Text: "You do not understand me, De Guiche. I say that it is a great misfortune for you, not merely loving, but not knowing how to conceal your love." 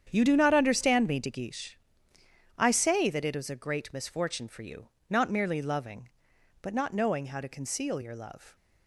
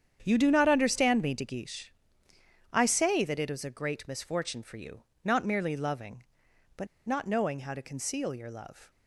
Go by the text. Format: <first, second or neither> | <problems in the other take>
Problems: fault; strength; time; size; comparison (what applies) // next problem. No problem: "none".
first | starts louder than the rest; strong; until 1.2 s; 8.5 dB; strong in the first // pauses between "but" and "not"; slight; at 6.8 s; 0.20 s long